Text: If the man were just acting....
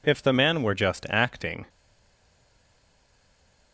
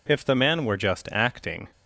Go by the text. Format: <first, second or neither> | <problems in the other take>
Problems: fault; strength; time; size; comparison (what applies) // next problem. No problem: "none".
second | stays silent after the last word; noticeable; from 1.6 s on; 2.1 s long